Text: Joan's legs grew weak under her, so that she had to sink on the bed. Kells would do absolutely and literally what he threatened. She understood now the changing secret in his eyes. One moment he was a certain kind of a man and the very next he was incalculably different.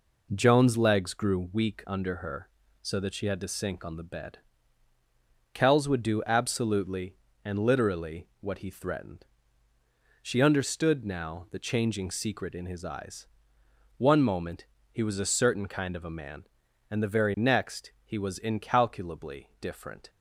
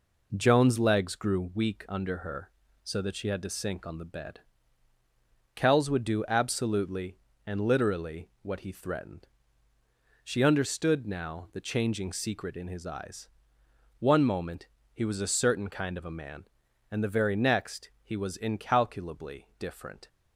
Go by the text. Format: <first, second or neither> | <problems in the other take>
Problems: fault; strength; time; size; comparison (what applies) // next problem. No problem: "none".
neither | pauses between "moment" and "he"; slight; the same in both